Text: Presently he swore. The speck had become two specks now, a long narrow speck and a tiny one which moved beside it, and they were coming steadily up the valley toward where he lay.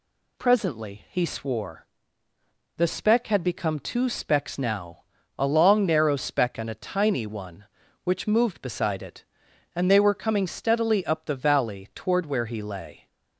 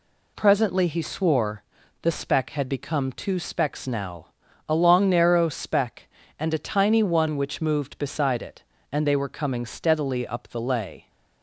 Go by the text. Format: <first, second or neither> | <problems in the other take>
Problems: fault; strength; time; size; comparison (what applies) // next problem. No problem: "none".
first | skips "valley toward where he"; at 10.6 s